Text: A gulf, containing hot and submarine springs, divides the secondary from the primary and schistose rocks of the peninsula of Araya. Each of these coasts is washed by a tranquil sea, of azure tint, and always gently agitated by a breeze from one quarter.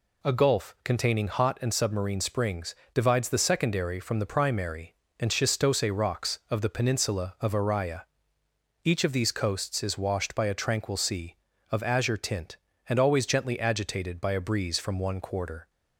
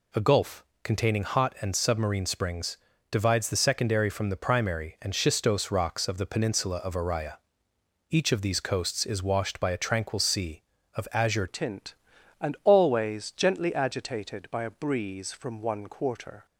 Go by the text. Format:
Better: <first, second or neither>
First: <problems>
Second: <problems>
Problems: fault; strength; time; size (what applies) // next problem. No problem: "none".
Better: first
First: none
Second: changes voice at "tint"; from 11.4 s on; 5.0 s long